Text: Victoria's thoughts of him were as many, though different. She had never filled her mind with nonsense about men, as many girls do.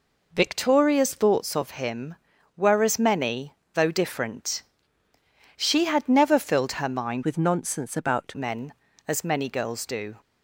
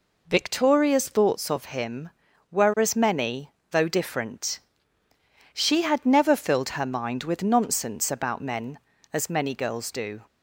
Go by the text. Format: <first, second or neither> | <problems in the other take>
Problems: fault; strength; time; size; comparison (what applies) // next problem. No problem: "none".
second | changes voice from "with" to "about"; from 7.2 to 8.3 s; 1.1 s long